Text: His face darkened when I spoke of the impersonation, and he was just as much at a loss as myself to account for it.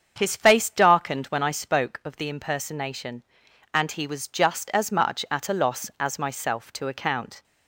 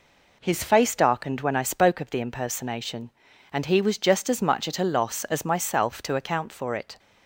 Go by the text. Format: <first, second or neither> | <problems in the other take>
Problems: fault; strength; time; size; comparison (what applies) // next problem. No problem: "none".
second | starts louder than the rest; strong; until 1.1 s; 7 dB // stops before "for it"; at 7.4 s